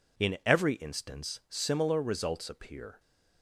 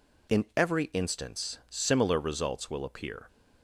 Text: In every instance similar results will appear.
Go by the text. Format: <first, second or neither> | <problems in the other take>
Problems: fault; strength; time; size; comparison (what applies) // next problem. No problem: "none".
second | skips "will"; at 2.4 s